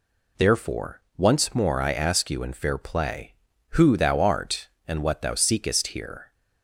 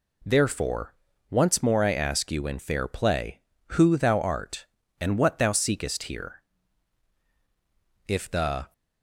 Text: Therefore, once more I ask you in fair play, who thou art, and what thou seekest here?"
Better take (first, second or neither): first